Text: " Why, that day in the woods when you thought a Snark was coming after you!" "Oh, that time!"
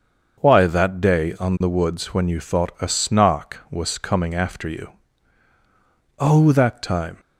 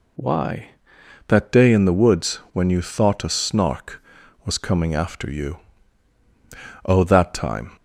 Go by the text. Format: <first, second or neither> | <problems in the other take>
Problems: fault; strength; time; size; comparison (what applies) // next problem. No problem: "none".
second | starts louder than the rest; until 1.4 s; 6.5 dB // says "on" for "in"; at 1.4 s